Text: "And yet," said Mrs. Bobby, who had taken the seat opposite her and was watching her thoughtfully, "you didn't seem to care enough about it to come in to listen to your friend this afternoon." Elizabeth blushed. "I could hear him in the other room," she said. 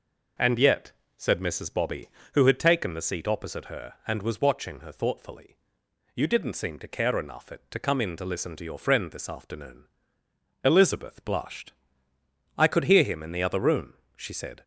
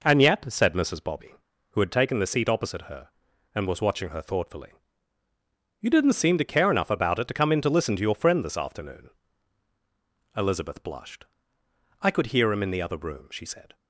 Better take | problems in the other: second | skips "about"; at 7.5 s

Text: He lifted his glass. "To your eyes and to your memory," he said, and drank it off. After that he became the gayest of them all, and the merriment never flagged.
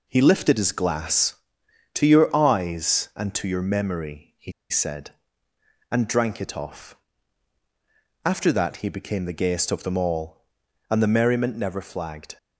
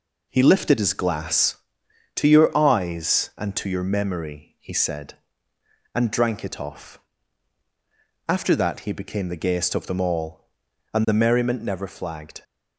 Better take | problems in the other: second | pauses between "he" and "said"; slight; at 4.5 s; 0.19 s long

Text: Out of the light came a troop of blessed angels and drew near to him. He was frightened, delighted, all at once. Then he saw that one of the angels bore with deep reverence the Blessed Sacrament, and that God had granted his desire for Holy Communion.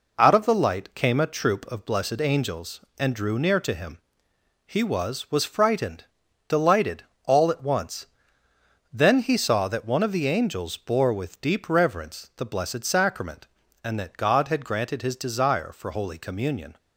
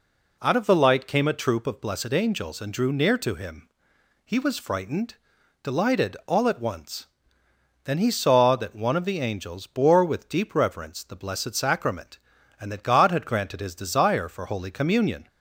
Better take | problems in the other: second | says "was" twice; at 5.2 s

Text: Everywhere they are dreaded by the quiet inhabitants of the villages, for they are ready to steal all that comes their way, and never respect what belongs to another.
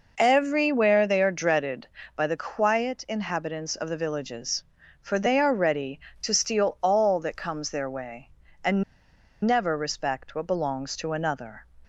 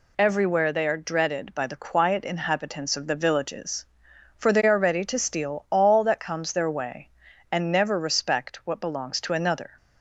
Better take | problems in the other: second | pauses between "and" and "never"; noticeable; at 8.8 s; 0.61 s long

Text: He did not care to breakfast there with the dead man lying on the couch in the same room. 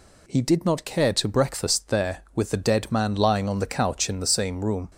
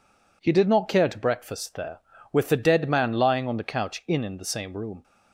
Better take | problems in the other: first | says "in" twice; at 4.2 s

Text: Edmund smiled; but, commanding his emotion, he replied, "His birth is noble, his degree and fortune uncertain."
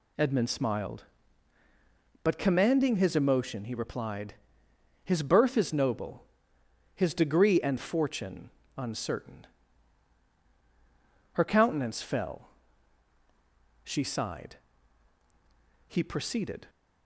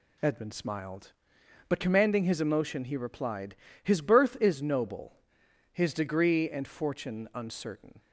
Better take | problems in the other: second | pauses between "fortune" and "uncertain"; slight; at 8.5 s; 0.26 s long // goes on to say "Her countenance fell she sighed he proceeded"; strong; from 11.3 s on; 5.3 s long

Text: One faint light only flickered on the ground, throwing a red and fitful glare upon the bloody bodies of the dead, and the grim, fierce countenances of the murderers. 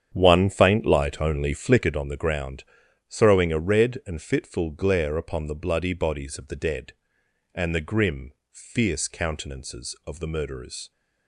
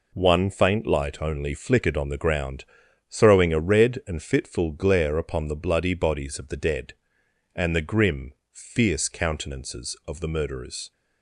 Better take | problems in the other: second | starts louder than the rest; strong; until 2.0 s; 8.5 dB

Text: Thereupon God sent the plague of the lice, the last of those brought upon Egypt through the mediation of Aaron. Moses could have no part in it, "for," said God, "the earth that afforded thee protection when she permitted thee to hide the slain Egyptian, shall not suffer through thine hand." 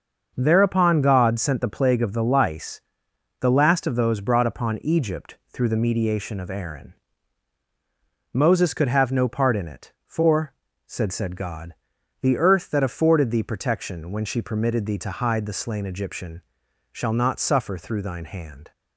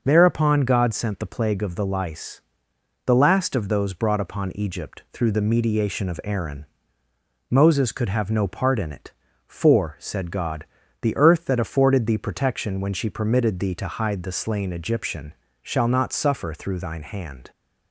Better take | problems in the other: second | starts louder than the rest; until 1.3 s; 6.5 dB // says "said" twice; at 11.1 s

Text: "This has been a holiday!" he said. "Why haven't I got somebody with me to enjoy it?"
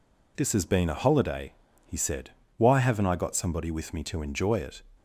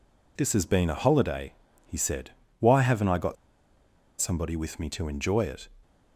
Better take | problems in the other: first | pauses between "got" and "somebody"; noticeable; at 3.3 s; 0.85 s long

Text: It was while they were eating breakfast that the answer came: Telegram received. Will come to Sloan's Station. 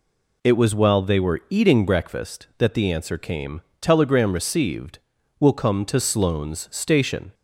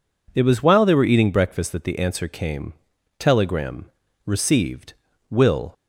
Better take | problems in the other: first | pauses between "Telegram" and "received"; at 3.8 s; 0.38 s long // stops before "come to Sloan's Station"; at 5.7 s

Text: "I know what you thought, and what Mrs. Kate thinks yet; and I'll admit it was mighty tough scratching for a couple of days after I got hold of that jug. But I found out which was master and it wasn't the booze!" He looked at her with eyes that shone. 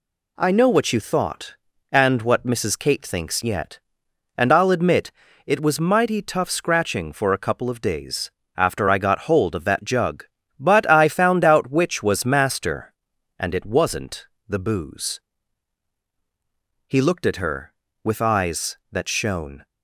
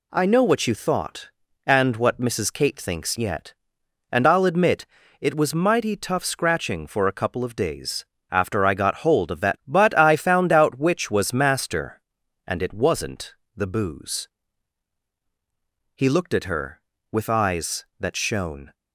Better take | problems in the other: first | pauses between "admit" and "it"; slight; at 4.8 s; 0.34 s long; slight in the first // pauses between "days" and "after"; slight; at 8.0 s; 0.26 s long; slight in the first // skips "jug"; at 9.6 s // pauses between "wasn't" and "the"; slight; at 13.3 s; 0.20 s long; slight in the first

